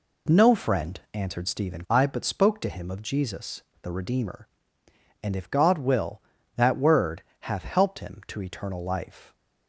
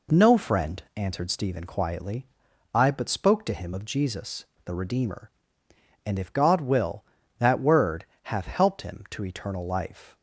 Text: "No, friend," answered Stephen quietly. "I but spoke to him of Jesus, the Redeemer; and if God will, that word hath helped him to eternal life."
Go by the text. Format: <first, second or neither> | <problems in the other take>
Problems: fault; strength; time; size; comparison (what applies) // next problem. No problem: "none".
second | skips "quietly"; at 1.8 s // pauses between "word" and "hath"; slight; at 7.2 s; 0.18 s long; slight in the second